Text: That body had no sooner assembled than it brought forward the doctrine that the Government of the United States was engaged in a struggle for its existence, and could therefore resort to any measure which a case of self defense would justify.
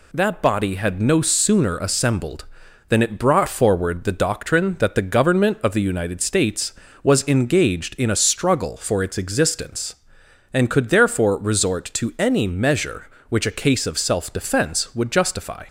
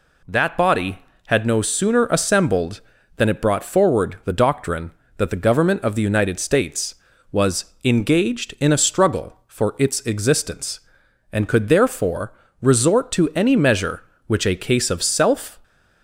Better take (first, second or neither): first